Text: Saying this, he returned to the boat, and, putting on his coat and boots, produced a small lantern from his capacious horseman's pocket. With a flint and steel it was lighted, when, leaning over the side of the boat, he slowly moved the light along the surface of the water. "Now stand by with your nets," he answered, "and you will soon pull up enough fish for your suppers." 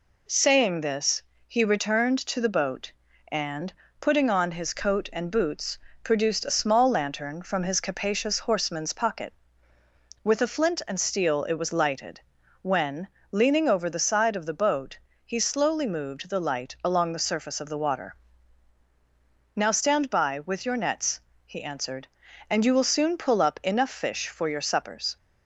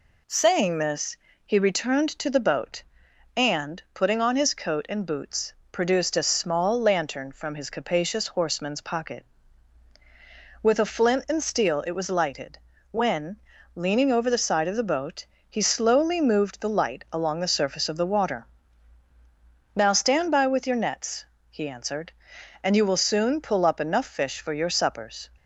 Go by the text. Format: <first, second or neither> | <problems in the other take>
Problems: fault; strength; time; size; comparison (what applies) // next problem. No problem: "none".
neither | none